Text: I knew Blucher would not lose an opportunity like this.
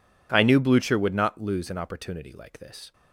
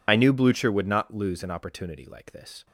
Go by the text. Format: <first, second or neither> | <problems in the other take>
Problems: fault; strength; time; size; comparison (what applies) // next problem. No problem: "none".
first | loses the start of "I"; at 0.0 s; 55 ms